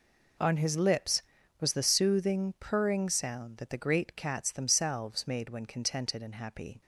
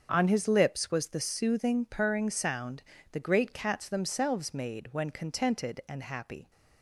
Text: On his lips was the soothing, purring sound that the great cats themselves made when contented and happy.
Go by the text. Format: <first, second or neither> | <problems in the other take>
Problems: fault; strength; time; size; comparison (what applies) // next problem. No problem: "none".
first | starts louder than the rest; until 1.1 s; 7 dB // skips "that"; at 2.9 s